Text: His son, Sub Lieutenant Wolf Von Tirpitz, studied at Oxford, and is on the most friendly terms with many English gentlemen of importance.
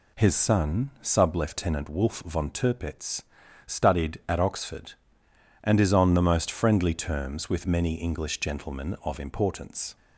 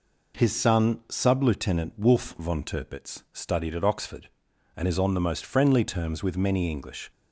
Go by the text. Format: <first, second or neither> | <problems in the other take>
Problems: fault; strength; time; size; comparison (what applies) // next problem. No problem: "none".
first | stops before "gentlemen of importance"; at 7.1 s